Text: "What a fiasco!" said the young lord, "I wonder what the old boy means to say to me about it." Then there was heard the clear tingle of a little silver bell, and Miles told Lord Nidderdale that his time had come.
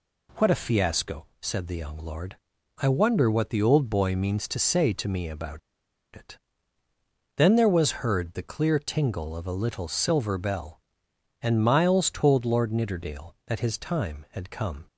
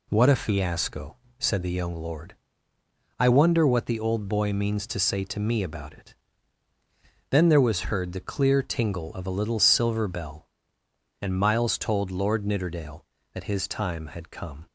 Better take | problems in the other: second | pauses between "about" and "it"; noticeable; at 5.5 s; 0.55 s long

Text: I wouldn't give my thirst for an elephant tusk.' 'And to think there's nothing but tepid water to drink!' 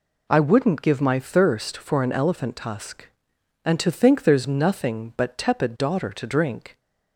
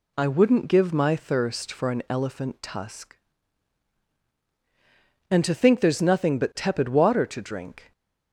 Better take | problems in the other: second | says "daughter" for "water"; at 5.7 s

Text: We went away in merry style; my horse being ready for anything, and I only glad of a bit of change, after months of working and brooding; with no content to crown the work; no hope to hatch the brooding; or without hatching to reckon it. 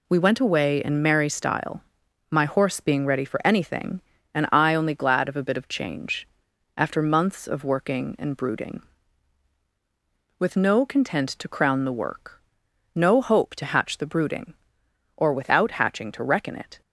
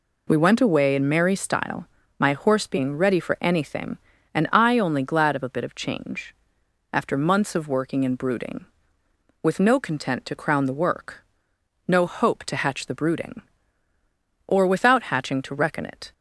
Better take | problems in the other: neither | none

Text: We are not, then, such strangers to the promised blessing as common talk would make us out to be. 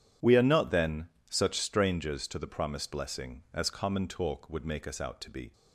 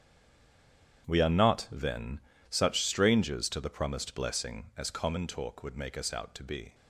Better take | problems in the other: first | stays silent before the first word; until 1.0 s; 1.0 s long // starts louder than the rest; strong; until 2.1 s; 9.5 dB

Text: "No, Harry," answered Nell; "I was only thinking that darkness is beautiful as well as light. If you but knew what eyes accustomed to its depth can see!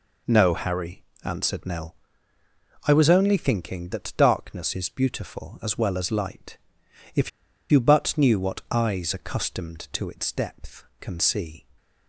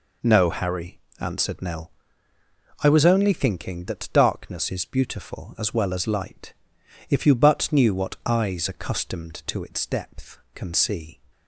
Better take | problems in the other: second | pauses between "If" and "you"; at 7.2 s; 0.42 s long

